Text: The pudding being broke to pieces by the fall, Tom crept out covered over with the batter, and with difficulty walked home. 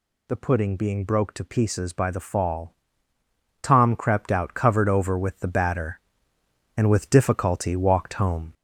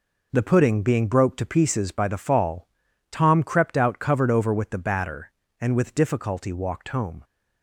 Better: second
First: gets louder; throughout; 3.5 dB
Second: none

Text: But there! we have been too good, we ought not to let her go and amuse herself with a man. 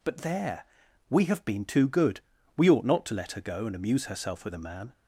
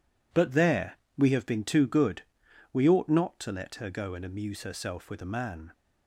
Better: neither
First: none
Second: none

